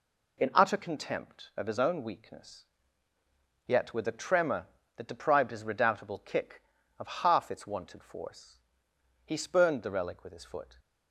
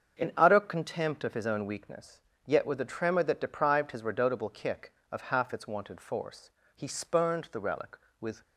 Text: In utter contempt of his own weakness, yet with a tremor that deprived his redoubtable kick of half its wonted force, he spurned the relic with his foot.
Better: first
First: none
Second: starts louder than the rest; until 1.2 s; 7 dB // stops before "his foot"; at 8.4 s

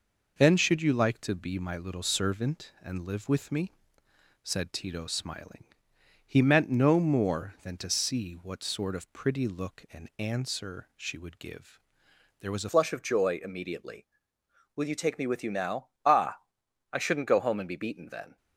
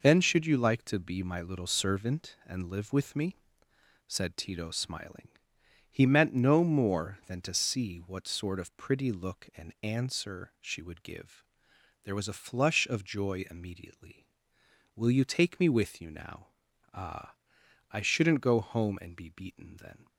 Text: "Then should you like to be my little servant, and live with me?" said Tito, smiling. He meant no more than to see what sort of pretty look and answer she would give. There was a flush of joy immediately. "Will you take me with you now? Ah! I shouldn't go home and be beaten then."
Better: second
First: changes voice at "flush"; from 12.7 s on; 5.6 s long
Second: none

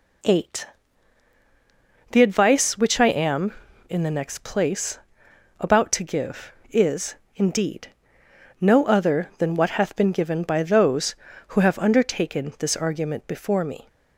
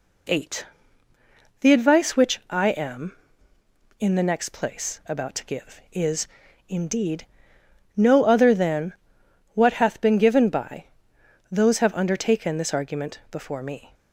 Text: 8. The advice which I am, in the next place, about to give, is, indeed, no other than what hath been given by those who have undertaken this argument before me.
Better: first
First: none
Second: pauses between "than" and "what"; noticeable; at 8.9 s; 0.62 s long // pauses between "by" and "those"; noticeable; at 10.8 s; 0.66 s long // skips "who"; at 11.7 s

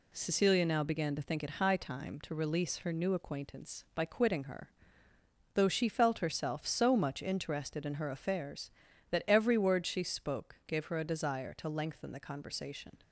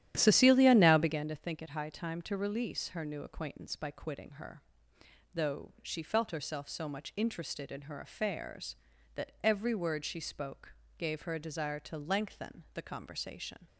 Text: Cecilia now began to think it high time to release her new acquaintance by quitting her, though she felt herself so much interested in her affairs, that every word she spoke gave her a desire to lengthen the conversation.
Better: first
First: none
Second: starts louder than the rest; strong; until 1.3 s; 11.5 dB // pauses between "spoke" and "gave"; slight; at 10.7 s; 0.24 s long

